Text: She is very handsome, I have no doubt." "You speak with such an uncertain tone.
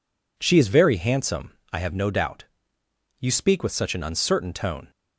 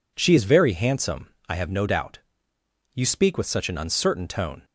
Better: neither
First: none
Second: none

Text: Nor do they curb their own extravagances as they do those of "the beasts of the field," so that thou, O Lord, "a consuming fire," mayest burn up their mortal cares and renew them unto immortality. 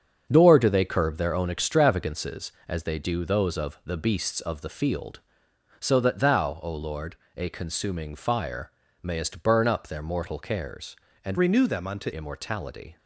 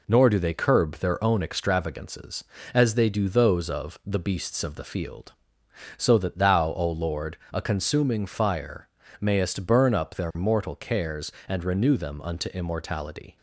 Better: second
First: starts louder than the rest; until 1.3 s; 7 dB // changes voice from "renew" to "unto"; from 11.3 to 12.0 s; 0.7 s long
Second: none

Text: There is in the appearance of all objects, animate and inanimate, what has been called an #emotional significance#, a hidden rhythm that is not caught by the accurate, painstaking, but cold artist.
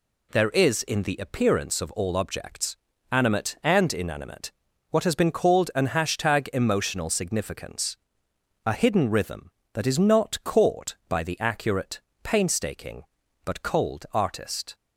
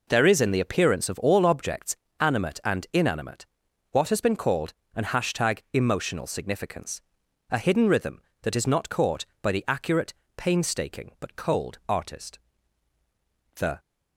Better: first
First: none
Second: pauses between "called" and "an"; slight; at 4.7 s; 0.22 s long // goes on to say "The"; slight; from 13.5 s on; 0.24 s long

